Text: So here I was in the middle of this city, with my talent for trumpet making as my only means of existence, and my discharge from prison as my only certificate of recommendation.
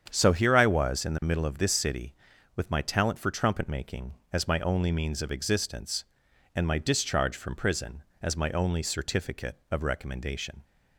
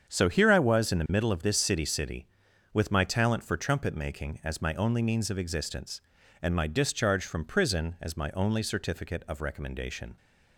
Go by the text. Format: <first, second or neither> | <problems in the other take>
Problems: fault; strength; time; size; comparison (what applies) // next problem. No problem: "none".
first | starts louder than the rest; strong; until 1.1 s; 7.5 dB; strong in the first // says "city" twice; at 1.8 s